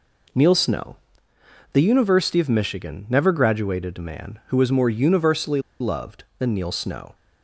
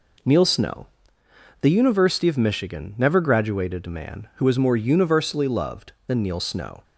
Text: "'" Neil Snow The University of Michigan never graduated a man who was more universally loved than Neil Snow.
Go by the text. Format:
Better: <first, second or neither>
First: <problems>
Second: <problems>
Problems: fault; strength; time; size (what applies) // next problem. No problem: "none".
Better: second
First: pauses between "Snow" and "The"; noticeable; at 0.9 s; 0.76 s long // pauses between "universally" and "loved"; slight; at 5.6 s; 0.18 s long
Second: pauses between "Snow" and "The"; noticeable; at 0.8 s; 0.74 s long